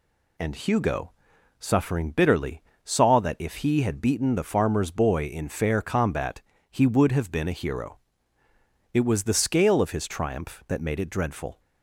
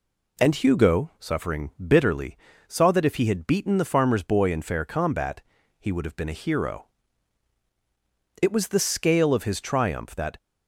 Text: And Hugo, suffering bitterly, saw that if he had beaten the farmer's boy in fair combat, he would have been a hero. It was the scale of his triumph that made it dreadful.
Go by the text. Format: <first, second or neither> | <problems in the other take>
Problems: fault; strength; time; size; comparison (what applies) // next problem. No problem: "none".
first | stops before "made it dreadful"; at 10.3 s